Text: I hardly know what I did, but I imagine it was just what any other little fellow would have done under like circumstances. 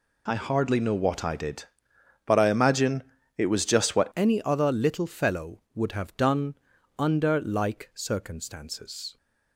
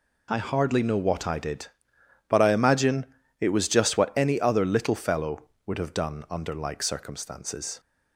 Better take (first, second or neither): second